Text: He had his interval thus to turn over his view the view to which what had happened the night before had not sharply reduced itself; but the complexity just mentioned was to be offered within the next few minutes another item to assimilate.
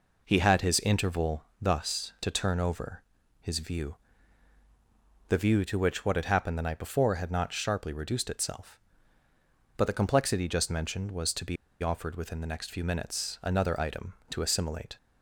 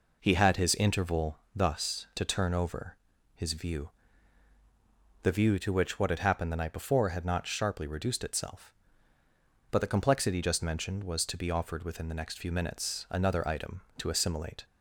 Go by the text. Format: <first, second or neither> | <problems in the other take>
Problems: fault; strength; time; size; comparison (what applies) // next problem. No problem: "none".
second | pauses between "interval" and "thus"; slight; at 1.4 s; 0.16 s long; slight in the second // pauses between "over" and "his"; at 3.0 s; 0.38 s long; also in the second // pauses between "view" and "the"; strong; at 3.9 s; 1.3 s long; strong in the second // pauses between "be" and "offered"; slight; at 11.5 s; 0.26 s long